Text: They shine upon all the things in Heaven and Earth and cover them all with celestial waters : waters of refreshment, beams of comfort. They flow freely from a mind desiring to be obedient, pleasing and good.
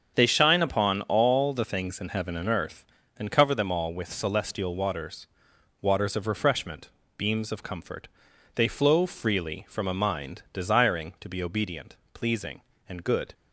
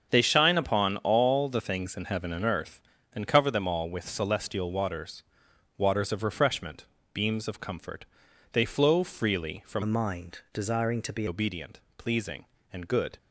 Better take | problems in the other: first | starts louder than the rest; until 1.1 s; 7 dB; also in the first // changes voice from "a" to "be"; from 9.8 to 11.2 s; 1.4 s long

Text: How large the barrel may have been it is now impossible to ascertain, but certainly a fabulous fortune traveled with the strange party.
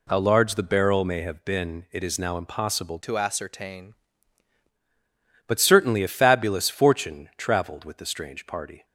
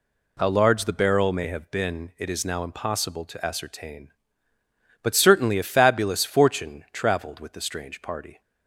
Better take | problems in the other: second | changes voice from "to" to "ascertain"; from 3.0 to 3.9 s; 0.9 s long

